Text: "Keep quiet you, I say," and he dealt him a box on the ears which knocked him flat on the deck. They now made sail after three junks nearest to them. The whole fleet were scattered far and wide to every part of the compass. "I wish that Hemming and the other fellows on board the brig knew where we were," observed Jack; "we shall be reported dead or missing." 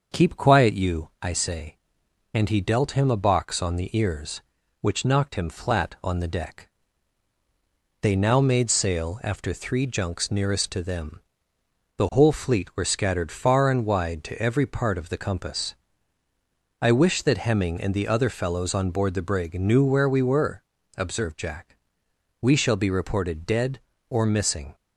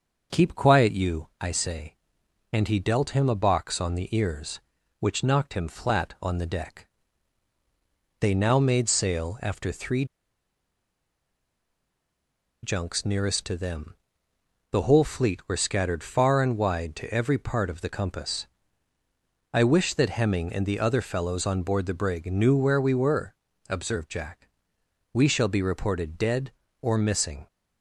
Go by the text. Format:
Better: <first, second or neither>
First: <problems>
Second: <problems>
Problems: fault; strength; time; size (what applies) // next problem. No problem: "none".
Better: first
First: starts louder than the rest; noticeable; until 1.2 s; 6 dB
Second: starts louder than the rest; noticeable; until 1.4 s; 6 dB // pauses between "three" and "junks"; strong; at 10.0 s; 2.5 s long